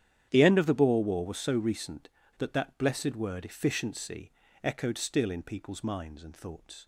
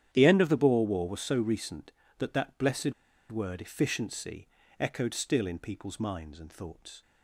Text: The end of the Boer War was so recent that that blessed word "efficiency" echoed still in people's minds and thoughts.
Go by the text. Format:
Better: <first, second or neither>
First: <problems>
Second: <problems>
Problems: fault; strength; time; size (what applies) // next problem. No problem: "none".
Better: first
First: starts louder than the rest; strong; until 1.3 s; 10 dB // pauses between "efficiency" and "echoed"; slight; at 4.3 s; 0.32 s long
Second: starts louder than the rest; strong; until 1.1 s; 10 dB // pauses between "blessed" and "word"; at 2.9 s; 0.38 s long // pauses between "efficiency" and "echoed"; slight; at 4.4 s; 0.32 s long